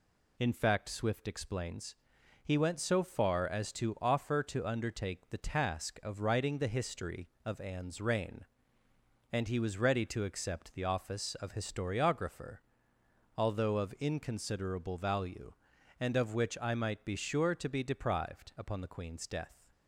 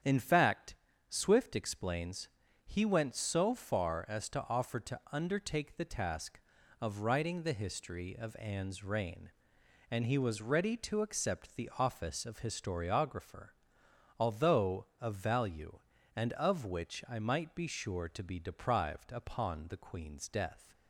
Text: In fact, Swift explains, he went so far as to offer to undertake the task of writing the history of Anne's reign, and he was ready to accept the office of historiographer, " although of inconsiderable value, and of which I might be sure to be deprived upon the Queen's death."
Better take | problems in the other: first | starts louder than the rest; strong; until 1.3 s; 8.5 dB // skips "inconsiderable"; at 15.1 s

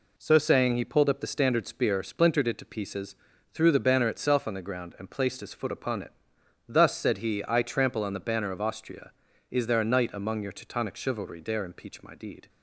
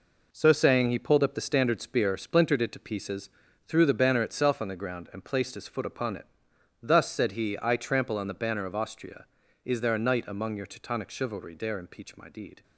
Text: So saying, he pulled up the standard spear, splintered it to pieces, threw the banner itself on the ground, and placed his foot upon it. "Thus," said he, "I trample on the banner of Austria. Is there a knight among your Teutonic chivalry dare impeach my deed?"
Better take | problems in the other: first | gets quieter; strong; throughout; 8 dB

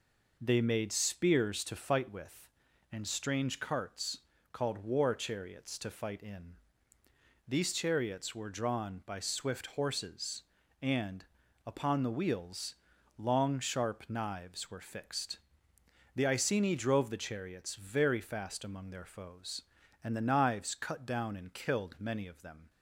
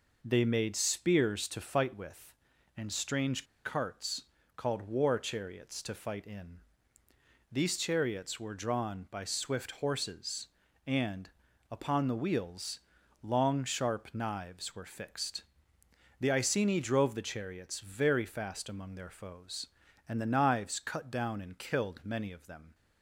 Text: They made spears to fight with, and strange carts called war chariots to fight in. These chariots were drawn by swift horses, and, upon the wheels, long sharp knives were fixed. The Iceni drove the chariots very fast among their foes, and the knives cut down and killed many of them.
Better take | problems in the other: first | pauses between "strange" and "carts"; slight; at 3.4 s; 0.19 s long // pauses between "carts" and "called"; slight; at 4.2 s; 0.34 s long; slight in the first

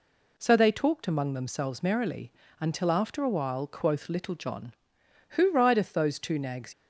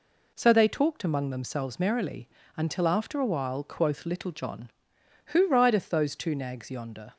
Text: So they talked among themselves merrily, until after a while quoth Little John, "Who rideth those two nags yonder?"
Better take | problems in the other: second | stops before "yonder"; at 6.7 s

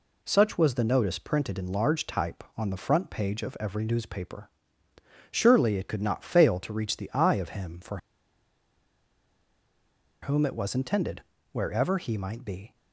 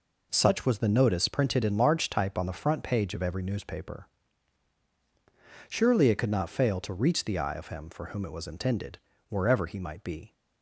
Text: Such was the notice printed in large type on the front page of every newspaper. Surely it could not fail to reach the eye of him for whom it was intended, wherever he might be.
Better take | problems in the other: second | pauses between "for" and "whom"; strong; at 7.9 s; 2.2 s long

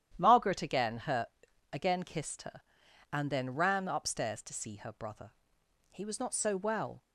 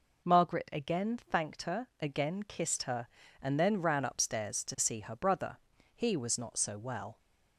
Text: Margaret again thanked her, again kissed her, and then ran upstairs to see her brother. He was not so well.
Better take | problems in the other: second | starts louder than the rest; strong; until 1.1 s; 10.5 dB // skips "thanked"; at 0.9 s

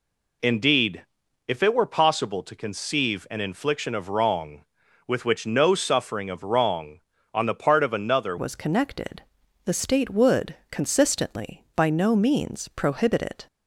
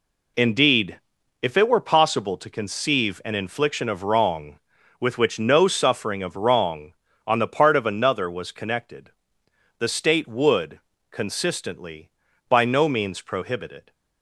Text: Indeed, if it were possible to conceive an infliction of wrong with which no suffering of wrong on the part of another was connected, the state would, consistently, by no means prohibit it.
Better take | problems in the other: second | changes voice at "was"; from 8.3 s on; 5.1 s long

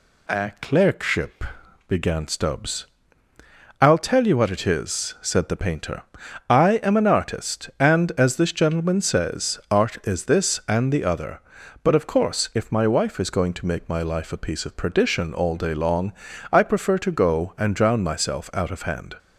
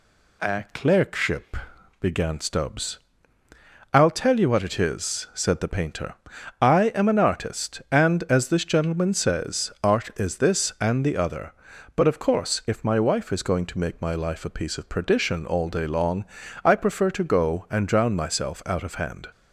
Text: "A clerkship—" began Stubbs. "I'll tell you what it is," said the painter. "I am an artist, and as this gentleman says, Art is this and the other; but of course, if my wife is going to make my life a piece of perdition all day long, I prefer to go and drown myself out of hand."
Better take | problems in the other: neither | none

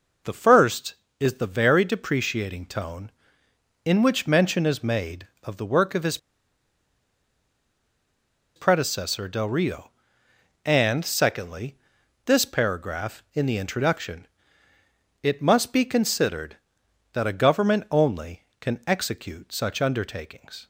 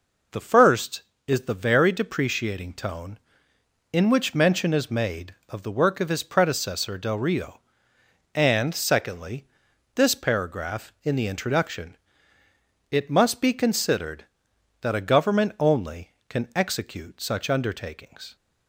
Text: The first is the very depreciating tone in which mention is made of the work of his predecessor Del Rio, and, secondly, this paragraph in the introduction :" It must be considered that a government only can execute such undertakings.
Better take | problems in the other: second | pauses between "his" and "predecessor"; strong; at 6.1 s; 2.3 s long

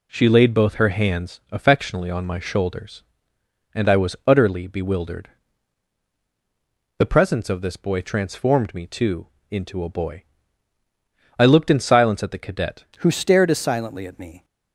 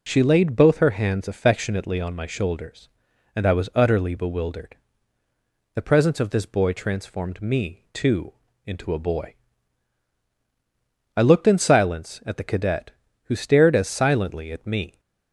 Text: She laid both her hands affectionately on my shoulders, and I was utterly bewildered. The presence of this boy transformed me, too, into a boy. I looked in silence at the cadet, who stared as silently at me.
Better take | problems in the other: second | changes voice at "who"; from 12.9 s on; 1.5 s long

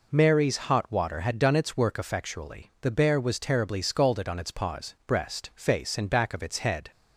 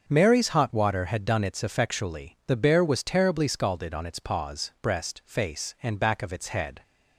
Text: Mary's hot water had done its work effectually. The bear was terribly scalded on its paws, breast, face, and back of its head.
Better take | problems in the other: first | starts louder than the rest; until 1.0 s; 6.5 dB // skips "work"; at 1.6 s

